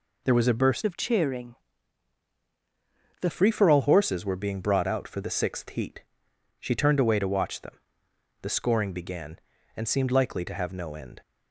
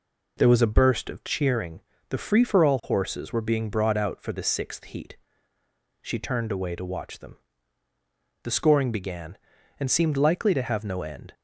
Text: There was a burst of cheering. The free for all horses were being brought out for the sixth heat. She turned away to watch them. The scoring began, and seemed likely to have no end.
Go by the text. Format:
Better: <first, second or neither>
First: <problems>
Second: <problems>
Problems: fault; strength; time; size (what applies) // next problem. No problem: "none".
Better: second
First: changes voice from "of" to "The"; from 0.8 to 3.2 s; 2.4 s long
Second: none